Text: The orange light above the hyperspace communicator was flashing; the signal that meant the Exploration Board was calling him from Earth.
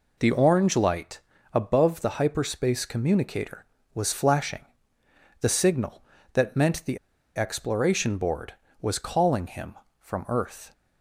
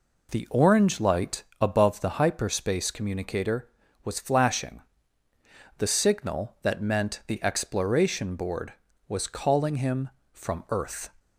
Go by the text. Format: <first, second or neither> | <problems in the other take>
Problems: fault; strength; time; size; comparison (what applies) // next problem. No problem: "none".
second | pauses between "light" and "above"; slight; at 1.2 s; 0.32 s long; slight in the second // pauses between "the" and "Exploration"; at 6.9 s; 0.37 s long